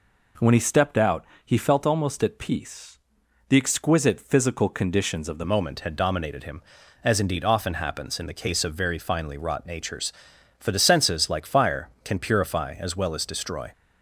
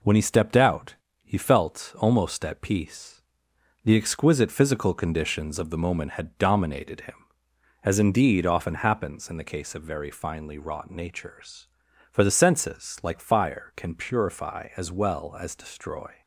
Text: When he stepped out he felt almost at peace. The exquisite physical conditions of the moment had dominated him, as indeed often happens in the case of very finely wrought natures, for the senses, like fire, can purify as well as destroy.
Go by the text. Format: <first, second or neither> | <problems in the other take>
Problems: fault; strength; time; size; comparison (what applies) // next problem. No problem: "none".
second | pauses between "out" and "he"; slight; at 1.2 s; 0.20 s long; slight in the second // changes voice at "moment"; from 5.4 s on; 8.3 s long